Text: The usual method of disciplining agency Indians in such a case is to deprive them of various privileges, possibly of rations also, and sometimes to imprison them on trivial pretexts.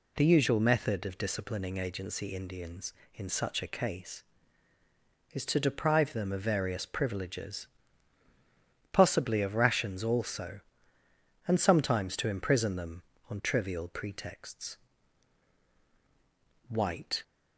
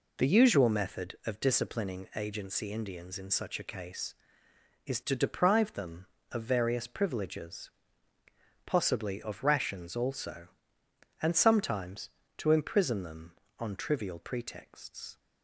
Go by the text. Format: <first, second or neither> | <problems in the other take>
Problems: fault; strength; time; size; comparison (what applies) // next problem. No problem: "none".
second | goes on to say "White"; from 16.6 s on; 0.54 s long